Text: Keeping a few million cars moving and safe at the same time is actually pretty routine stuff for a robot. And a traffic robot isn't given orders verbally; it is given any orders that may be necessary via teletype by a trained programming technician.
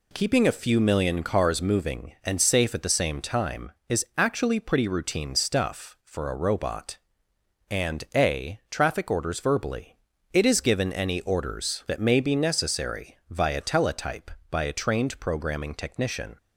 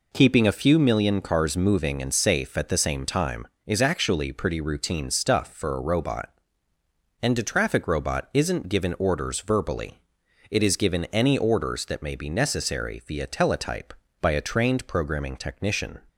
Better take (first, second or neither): second